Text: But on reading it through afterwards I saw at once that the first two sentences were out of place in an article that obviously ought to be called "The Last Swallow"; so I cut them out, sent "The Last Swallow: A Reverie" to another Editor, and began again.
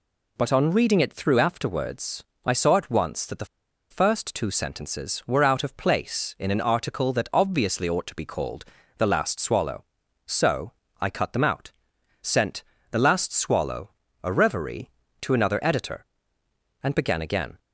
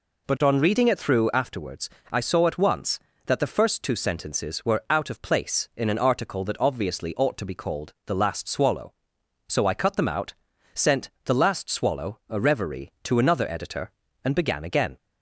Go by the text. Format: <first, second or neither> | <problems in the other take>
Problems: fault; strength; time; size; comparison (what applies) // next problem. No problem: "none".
second | pauses between "afterwards" and "I"; slight; at 2.2 s; 0.22 s long; slight in the second // pauses between "the" and "first"; at 3.4 s; 0.45 s long // pauses between "called" and "The"; slight; at 8.6 s; 0.32 s long // pauses between "so" and "I"; slight; at 10.7 s; 0.26 s long // pauses between "sent" and "The"; slight; at 12.6 s; 0.28 s long; slight in the second